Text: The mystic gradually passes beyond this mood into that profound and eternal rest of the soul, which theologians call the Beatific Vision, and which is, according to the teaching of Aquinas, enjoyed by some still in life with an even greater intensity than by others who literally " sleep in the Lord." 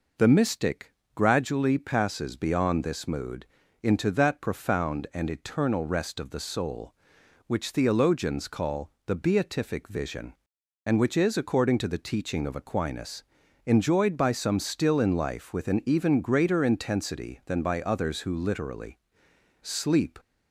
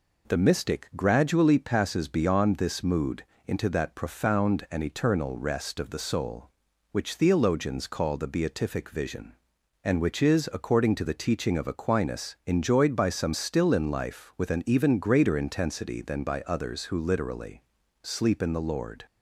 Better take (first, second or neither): second